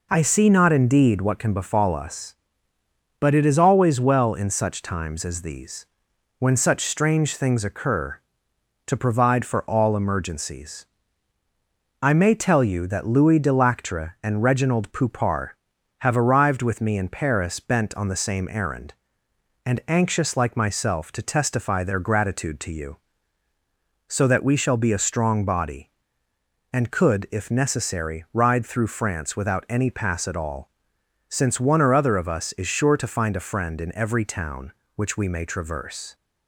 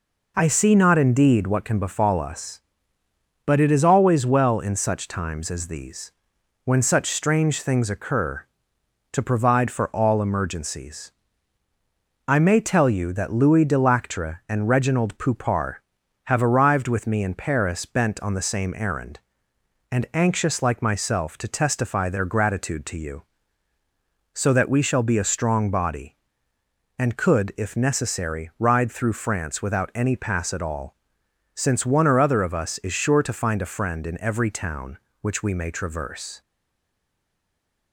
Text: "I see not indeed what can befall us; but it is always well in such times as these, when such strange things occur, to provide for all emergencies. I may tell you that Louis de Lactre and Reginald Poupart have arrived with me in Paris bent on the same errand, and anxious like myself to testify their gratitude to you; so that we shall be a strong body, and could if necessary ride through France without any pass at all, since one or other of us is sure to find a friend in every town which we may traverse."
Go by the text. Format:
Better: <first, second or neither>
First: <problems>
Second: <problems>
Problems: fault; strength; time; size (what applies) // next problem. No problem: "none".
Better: first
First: none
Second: stays silent after the last word; noticeable; from 36.4 s on; 1.5 s long